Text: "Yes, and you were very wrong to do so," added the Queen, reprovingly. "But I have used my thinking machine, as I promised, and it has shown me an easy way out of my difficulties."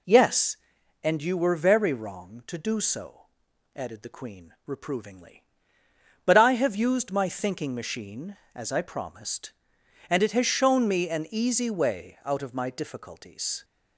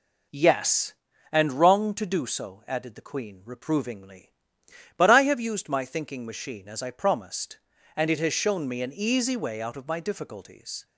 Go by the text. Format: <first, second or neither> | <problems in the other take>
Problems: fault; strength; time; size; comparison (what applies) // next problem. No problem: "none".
first | skips "you were very"; at 1.5 s